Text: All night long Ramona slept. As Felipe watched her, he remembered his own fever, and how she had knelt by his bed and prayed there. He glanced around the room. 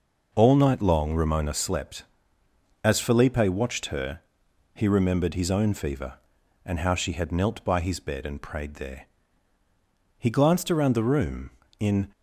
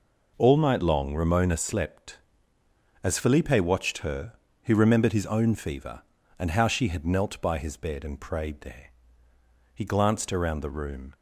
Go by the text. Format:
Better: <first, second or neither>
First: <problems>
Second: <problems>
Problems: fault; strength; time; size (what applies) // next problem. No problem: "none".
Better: second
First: goes on to say "In"; slight; from 11.7 s on; 0.30 s long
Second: none